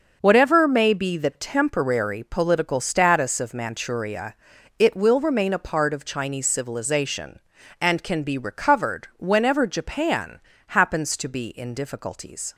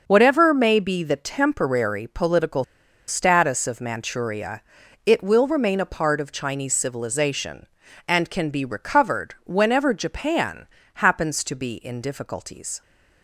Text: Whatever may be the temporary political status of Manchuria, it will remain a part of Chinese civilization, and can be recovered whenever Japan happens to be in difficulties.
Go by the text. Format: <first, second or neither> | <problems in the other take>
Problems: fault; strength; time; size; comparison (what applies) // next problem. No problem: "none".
first | starts louder than the rest; until 1.0 s; 6.5 dB; also in the first // pauses between "political" and "status"; at 2.6 s; 0.45 s long // pauses between "Japan" and "happens"; slight; at 10.6 s; 0.30 s long; slight in the first